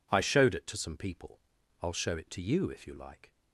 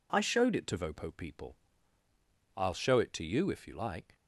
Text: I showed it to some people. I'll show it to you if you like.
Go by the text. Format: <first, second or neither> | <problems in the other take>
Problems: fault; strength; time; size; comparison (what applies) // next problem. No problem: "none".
first | says "vopo" for "some"; at 0.7 s